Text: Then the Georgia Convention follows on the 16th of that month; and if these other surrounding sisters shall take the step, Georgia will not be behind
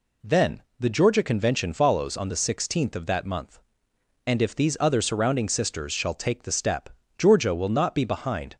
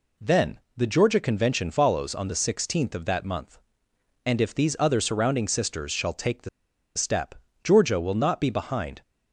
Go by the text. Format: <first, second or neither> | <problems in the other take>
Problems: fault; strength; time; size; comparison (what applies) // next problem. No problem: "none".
first | pauses between "Then" and "the"; slight; at 0.5 s; 0.18 s long; slight in the first // pauses between "the" and "step"; noticeable; at 6.4 s; 0.46 s long